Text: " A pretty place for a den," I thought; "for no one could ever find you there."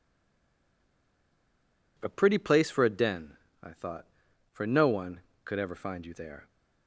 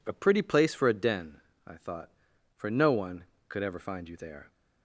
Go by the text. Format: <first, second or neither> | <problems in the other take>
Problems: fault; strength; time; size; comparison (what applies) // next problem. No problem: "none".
second | stays silent before the first word; noticeable; until 1.9 s; 1.9 s long